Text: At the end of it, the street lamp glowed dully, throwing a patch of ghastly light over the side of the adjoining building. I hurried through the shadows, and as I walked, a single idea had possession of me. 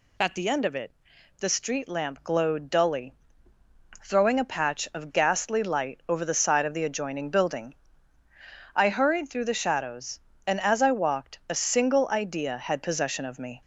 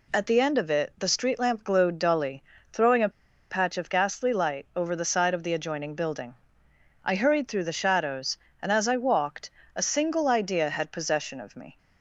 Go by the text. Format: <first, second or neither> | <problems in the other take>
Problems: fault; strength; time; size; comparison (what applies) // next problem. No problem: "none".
first | pauses between "a" and "patch"; at 3.1 s; 0.39 s long